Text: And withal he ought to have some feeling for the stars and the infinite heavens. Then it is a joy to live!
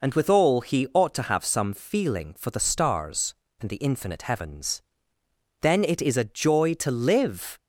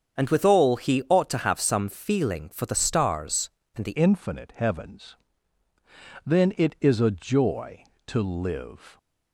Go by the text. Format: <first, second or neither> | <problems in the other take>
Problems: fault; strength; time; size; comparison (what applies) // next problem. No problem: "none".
first | starts louder than the rest; strong; until 1.2 s; 7.5 dB // changes voice at "infinite"; from 3.9 s on; 5.0 s long